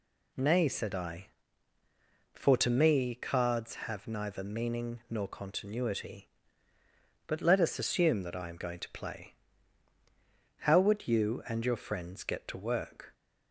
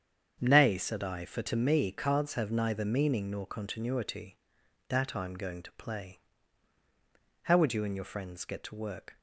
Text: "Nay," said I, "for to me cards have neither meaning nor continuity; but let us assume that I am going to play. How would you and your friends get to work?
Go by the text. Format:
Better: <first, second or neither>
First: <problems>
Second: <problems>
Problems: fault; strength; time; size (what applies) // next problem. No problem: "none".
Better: first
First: none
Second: starts louder than the rest; strong; until 1.4 s; 7.5 dB // skips "but let us assume"; at 4.6 s